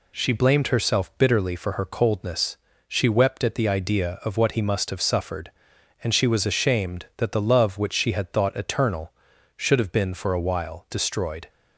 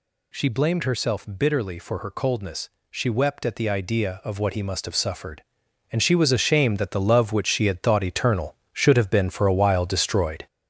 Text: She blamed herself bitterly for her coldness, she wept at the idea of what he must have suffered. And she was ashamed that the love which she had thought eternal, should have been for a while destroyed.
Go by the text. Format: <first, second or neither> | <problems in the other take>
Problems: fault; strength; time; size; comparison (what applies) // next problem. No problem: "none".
first | gets louder; noticeable; throughout; 4.5 dB